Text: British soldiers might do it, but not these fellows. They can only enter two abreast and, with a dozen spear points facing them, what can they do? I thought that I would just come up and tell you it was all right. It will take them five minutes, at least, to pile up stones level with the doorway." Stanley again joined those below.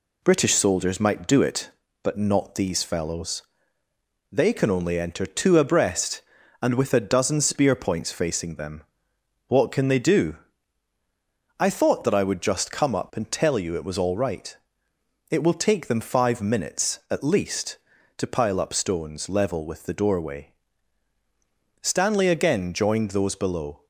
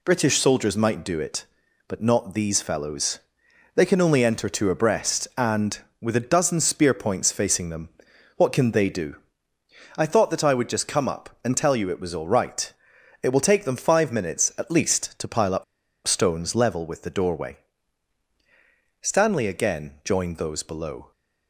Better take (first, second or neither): first